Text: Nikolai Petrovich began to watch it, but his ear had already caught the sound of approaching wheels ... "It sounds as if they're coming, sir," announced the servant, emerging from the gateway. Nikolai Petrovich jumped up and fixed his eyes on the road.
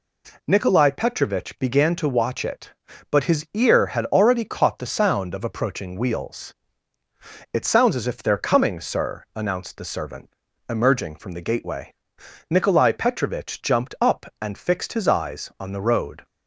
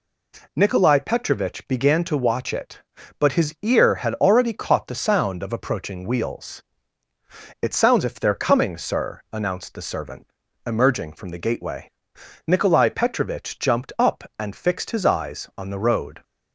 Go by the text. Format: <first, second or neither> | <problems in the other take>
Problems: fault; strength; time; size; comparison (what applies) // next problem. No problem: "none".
first | skips "as"; at 8.0 s